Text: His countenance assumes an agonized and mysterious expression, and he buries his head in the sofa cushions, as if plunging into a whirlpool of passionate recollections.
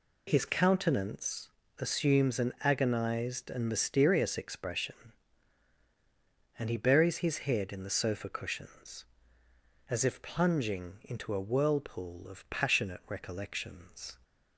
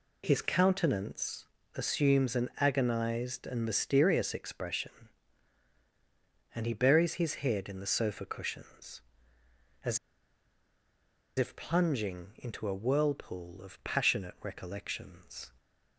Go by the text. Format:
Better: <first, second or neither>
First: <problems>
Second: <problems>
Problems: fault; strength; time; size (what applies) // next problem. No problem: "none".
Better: first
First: pauses between "countenance" and "assumes"; slight; at 1.4 s; 0.30 s long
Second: pauses between "countenance" and "assumes"; slight; at 1.4 s; 0.30 s long // pauses between "as" and "if"; strong; at 9.9 s; 1.3 s long